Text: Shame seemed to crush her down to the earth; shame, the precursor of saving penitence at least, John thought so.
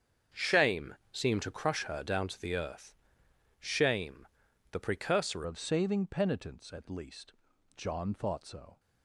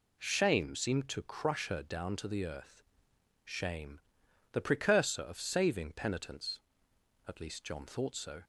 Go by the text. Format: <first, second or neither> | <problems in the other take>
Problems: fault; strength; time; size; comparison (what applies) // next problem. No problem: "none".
second | starts louder than the rest; strong; until 1.5 s; 7.5 dB // pauses between "Shame" and "seemed"; slight; at 0.9 s; 0.18 s long // changes voice at "of"; from 5.4 s on; 3.3 s long